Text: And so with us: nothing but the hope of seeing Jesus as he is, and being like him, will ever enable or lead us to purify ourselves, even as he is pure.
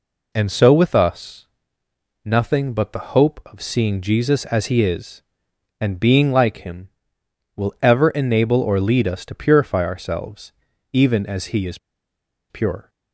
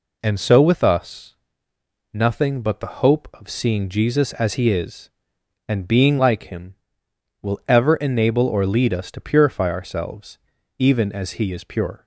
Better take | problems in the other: second | pauses between "is" and "pure"; noticeable; at 11.7 s; 0.73 s long

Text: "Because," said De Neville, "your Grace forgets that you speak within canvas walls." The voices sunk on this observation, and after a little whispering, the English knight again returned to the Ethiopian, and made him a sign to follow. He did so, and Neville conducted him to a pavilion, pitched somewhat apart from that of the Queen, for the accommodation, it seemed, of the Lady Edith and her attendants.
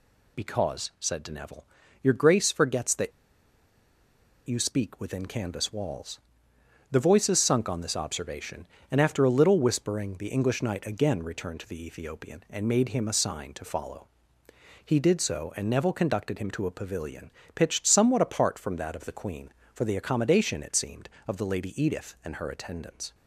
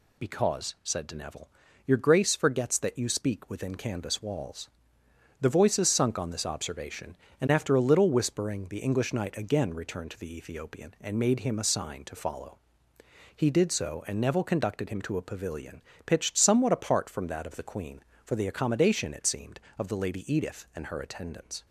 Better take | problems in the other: second | pauses between "that" and "you"; strong; at 3.1 s; 1.3 s long

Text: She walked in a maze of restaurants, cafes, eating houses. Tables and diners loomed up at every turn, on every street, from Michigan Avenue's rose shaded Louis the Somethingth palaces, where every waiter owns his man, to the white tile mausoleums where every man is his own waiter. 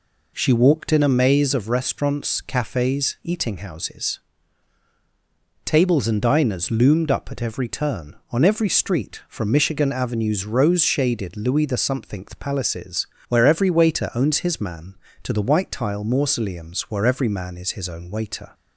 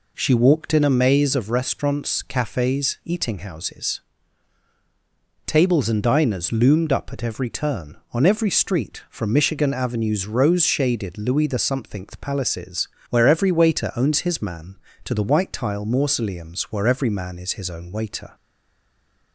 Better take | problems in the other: first | stays silent after the last word; from 18.3 s on; 1.0 s long

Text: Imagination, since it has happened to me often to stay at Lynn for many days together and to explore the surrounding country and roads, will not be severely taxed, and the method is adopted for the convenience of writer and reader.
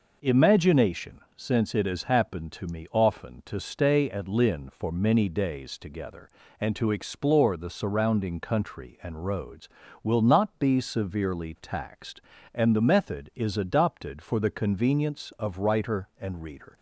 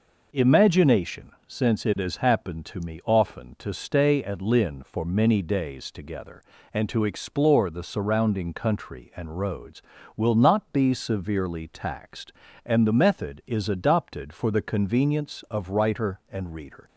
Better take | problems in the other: neither | none

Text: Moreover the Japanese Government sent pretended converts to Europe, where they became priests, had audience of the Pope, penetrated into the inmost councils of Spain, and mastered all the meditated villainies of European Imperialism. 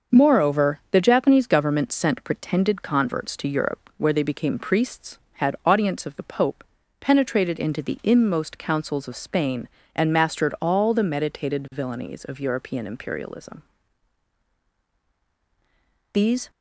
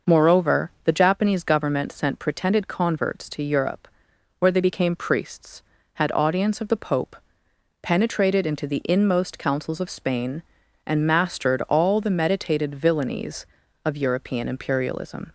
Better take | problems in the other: second | starts louder than the rest; until 1.2 s; 6.5 dB // goes on to say "These"; slight; from 16.1 s on; 0.38 s long

